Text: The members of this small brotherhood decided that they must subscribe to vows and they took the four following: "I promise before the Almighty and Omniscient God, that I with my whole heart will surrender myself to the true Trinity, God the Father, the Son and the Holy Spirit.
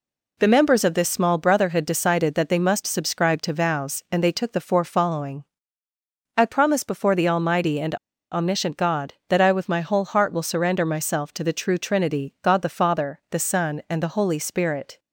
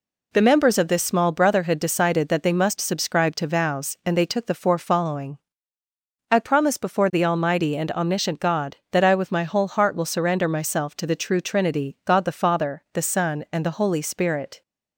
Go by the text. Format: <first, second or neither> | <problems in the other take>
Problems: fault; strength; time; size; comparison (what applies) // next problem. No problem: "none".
second | pauses between "and" and "Omniscient"; at 7.9 s; 0.36 s long